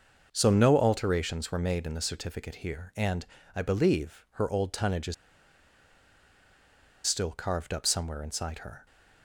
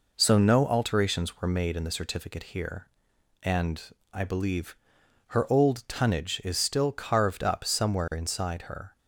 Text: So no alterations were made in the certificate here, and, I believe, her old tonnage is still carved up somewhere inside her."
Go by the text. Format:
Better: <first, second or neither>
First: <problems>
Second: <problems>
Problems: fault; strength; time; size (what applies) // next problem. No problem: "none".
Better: second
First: starts louder than the rest; until 1.3 s; 6.5 dB // pauses between "is" and "still"; strong; at 5.1 s; 1.9 s long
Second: none